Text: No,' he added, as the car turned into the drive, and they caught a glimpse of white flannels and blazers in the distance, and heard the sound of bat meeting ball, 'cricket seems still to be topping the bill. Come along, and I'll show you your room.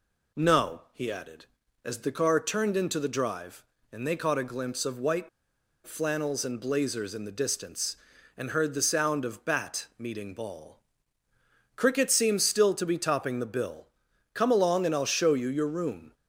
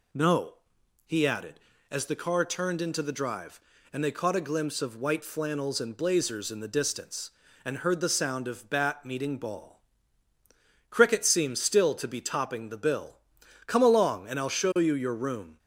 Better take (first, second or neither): second